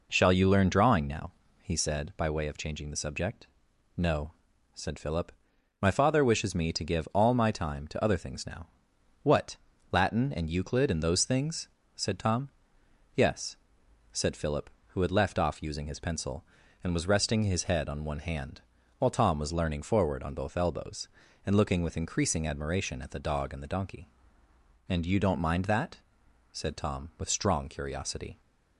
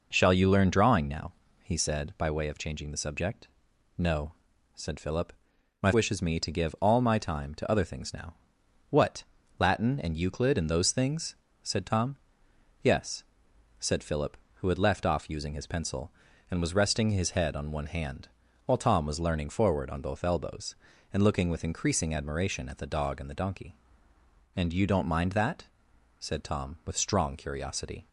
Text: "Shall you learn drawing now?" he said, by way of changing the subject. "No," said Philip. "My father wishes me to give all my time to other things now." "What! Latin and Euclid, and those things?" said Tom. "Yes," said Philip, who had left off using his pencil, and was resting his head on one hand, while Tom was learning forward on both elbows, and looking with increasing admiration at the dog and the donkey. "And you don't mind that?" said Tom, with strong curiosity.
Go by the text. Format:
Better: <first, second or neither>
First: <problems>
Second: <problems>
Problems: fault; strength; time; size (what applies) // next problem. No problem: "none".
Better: first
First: none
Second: skips "father"; at 5.9 s